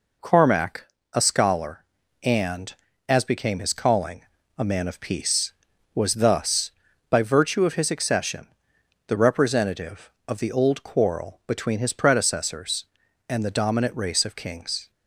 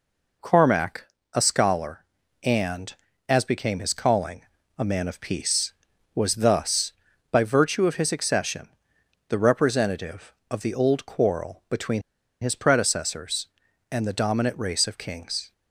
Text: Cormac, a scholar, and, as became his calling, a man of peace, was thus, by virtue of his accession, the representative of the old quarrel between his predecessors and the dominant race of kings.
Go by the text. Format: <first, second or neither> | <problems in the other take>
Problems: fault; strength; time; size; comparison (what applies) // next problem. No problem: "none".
first | pauses between "between" and "his"; at 12.0 s; 0.41 s long